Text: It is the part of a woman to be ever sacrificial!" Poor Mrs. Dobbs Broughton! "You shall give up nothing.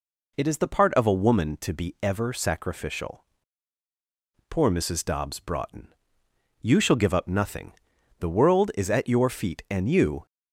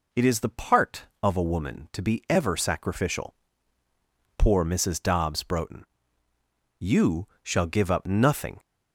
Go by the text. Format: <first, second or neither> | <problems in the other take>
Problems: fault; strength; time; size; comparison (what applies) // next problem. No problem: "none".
second | goes on to say "The world is at your feet and you"; strong; from 8.1 s on; 2.0 s long